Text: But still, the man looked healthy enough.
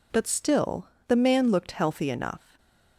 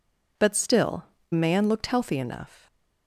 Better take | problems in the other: first | skips "the"; at 1.1 s

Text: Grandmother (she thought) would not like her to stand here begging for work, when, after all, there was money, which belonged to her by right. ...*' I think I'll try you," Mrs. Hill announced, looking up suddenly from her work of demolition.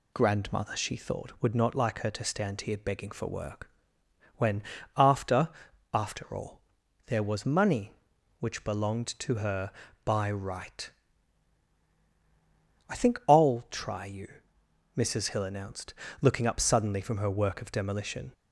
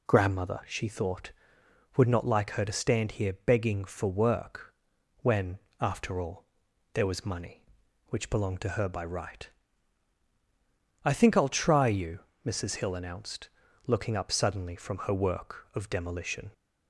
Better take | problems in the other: second | says "after" twice; at 5.9 s

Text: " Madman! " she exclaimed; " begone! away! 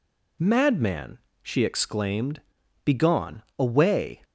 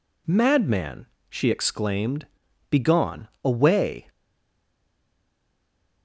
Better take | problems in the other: first | stays silent after the last word; noticeable; from 4.0 s on; 2.0 s long

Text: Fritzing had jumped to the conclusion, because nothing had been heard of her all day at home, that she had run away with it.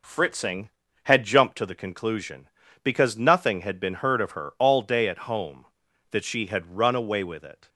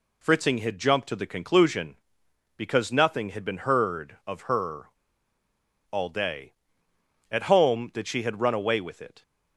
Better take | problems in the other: first | pauses between "her" and "all"; at 4.8 s; 1.0 s long

